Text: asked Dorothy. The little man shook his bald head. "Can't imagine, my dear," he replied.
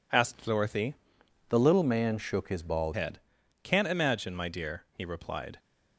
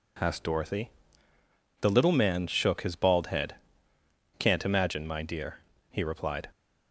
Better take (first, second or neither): second